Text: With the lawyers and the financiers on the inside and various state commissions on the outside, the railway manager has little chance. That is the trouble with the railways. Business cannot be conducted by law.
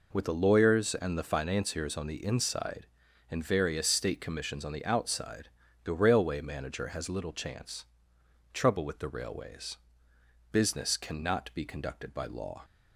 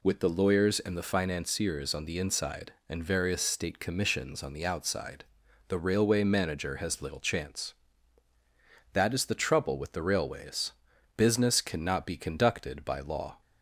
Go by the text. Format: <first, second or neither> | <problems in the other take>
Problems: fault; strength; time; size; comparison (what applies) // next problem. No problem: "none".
second | skips "That is the"; at 8.1 s